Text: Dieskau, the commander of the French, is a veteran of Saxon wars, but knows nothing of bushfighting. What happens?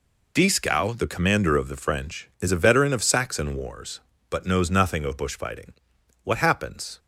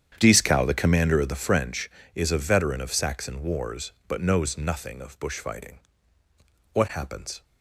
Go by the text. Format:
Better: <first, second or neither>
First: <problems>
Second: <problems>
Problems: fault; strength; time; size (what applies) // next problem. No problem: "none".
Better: first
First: none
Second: starts louder than the rest; strong; until 1.6 s; 9 dB